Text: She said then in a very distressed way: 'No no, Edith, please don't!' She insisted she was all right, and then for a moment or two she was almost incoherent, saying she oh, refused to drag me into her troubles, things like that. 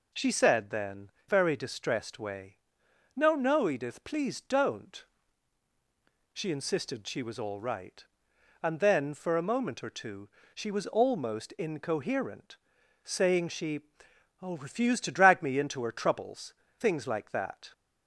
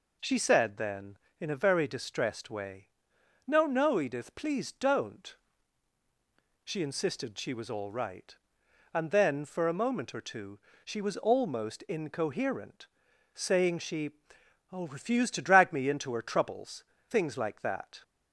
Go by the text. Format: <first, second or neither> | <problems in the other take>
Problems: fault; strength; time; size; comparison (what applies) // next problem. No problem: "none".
second | skips "in a"; at 1.1 s // pauses between "two" and "she"; slight; at 10.2 s; 0.24 s long; slight in the second // pauses between "she" and "oh"; noticeable; at 13.7 s; 0.64 s long; noticeable in the second